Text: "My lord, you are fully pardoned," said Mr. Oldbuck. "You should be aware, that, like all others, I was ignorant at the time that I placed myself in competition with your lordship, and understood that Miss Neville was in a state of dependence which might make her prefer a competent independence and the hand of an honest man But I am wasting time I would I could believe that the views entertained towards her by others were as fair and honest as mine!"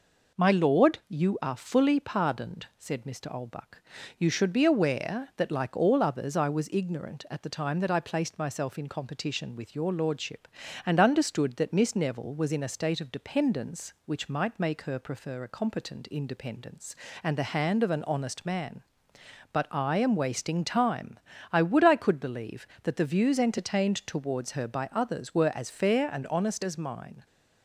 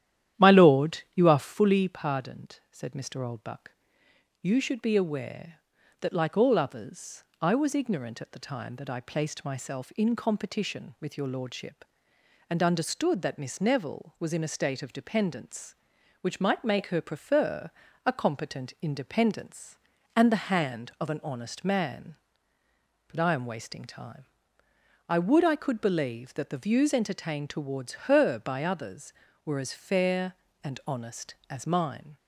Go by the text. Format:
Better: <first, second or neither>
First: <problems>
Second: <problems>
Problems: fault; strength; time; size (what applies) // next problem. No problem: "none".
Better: first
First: pauses between "time" and "I"; slight; at 21.1 s; 0.32 s long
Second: starts louder than the rest; strong; until 1.6 s; 11 dB // pauses between "prefer" and "a"; slight; at 17.7 s; 0.34 s long // pauses between "time" and "I"; noticeable; at 24.2 s; 0.84 s long